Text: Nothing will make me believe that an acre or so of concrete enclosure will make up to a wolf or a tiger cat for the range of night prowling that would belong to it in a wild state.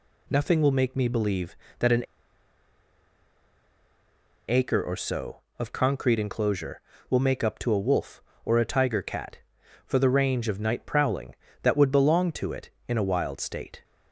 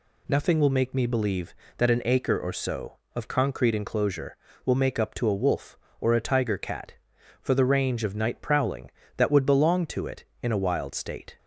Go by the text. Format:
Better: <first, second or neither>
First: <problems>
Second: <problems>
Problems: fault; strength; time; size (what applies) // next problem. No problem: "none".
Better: second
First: pauses between "an" and "acre"; strong; at 2.0 s; 2.4 s long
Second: none